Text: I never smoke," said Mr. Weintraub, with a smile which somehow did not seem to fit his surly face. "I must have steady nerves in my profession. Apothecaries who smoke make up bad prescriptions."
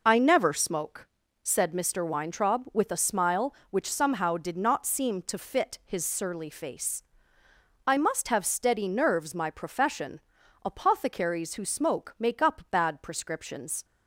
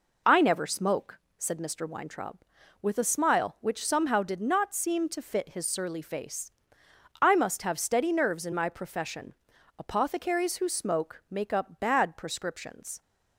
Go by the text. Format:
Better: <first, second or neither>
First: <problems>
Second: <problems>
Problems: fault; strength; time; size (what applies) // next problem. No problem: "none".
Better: second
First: skips "in"; at 9.3 s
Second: none